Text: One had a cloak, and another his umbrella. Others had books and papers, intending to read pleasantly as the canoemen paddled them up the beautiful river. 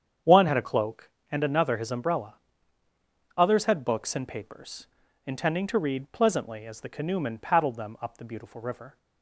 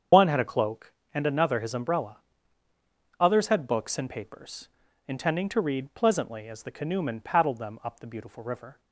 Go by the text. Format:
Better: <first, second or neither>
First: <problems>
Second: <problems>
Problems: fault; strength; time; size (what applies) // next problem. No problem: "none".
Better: first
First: starts louder than the rest; strong; until 1.4 s; 8 dB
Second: loses the start of "One"; at 0.1 s; 55 ms // starts louder than the rest; strong; until 1.3 s; 7.5 dB